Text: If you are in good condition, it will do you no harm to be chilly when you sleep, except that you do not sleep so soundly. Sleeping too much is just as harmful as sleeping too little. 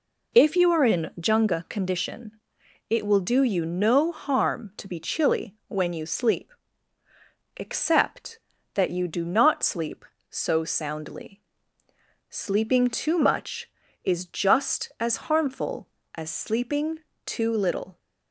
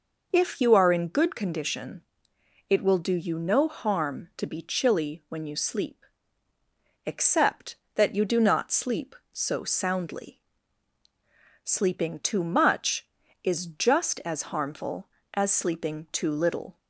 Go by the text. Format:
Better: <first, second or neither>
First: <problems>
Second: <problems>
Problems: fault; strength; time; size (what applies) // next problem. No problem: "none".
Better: second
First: says "junga" for "good"; at 1.2 s // pauses between "sleeping" and "too"; slight; at 17.0 s; 0.26 s long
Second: none